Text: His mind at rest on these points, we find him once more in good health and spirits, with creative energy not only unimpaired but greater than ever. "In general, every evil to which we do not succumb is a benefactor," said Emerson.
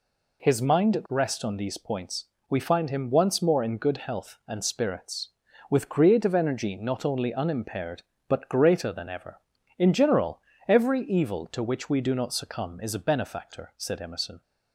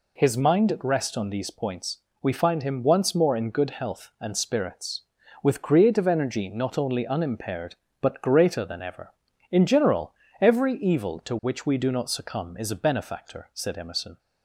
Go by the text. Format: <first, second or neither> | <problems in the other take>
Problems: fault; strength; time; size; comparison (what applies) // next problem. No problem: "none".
neither | none